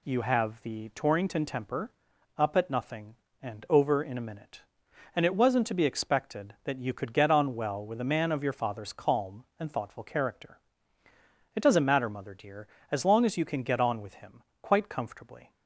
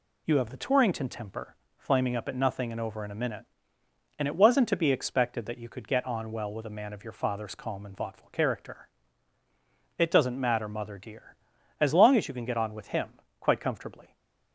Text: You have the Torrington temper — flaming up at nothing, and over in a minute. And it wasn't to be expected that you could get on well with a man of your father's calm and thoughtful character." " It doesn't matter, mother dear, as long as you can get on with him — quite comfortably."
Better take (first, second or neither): second